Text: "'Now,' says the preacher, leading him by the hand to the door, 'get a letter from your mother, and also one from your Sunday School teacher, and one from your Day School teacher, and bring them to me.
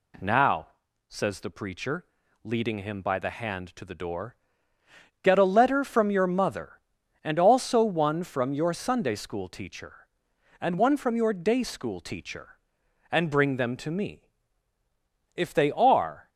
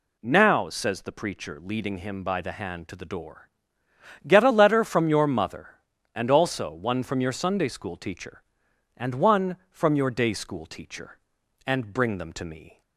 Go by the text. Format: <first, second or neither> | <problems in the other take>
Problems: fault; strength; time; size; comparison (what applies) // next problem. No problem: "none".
second | goes on to say "If they are"; noticeable; from 15.3 s on; 0.94 s long